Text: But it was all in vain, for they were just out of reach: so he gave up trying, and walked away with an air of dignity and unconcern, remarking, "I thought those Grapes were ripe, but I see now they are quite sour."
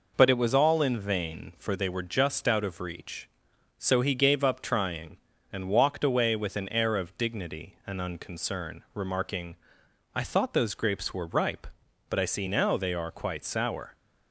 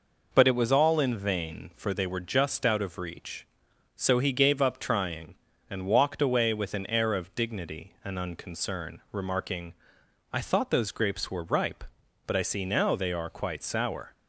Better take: neither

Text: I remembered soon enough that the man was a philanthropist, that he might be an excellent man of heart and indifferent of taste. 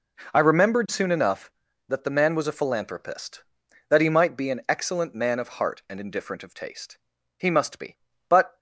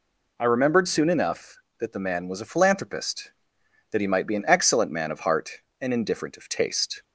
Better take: second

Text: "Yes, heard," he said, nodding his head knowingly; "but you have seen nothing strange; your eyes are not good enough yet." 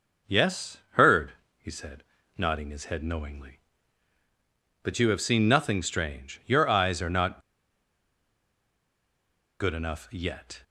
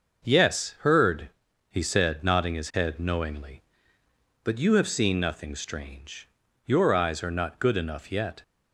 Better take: second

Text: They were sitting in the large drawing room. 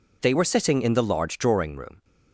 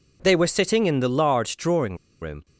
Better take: first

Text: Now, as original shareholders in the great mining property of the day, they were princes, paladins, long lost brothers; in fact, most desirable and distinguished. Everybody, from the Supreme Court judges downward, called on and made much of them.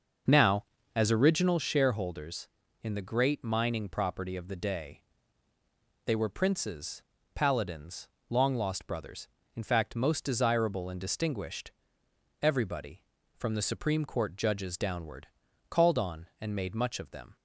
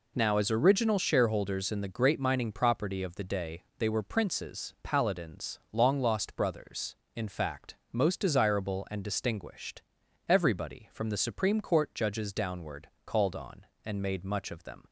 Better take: second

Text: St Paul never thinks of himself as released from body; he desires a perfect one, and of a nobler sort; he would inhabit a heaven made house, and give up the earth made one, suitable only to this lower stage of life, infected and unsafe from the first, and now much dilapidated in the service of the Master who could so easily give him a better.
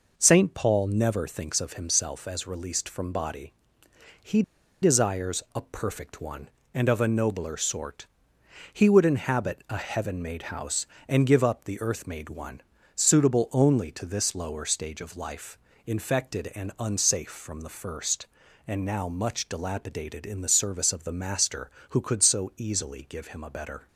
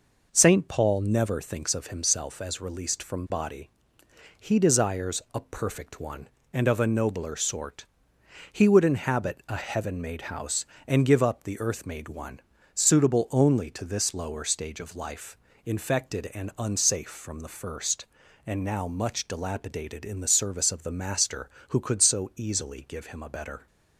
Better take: second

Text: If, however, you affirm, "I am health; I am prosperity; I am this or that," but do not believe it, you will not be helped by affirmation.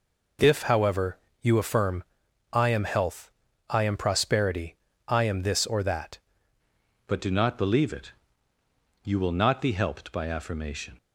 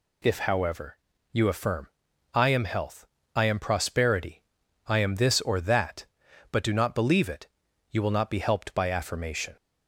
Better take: second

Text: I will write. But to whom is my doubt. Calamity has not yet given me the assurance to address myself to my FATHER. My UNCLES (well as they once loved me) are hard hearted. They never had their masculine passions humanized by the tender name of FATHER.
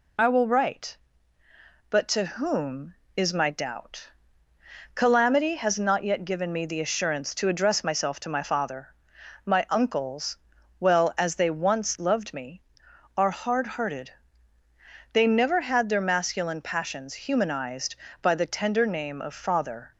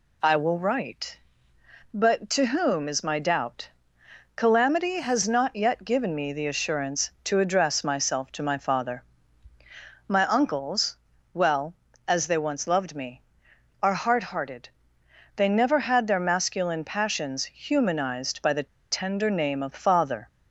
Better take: first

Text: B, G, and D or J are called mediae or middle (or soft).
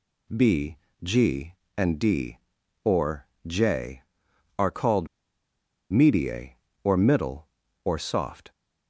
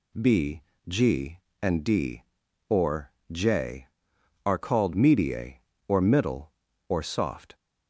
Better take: second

